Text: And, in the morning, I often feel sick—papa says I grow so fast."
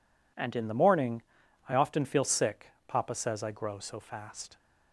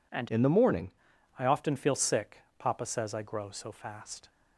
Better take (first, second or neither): first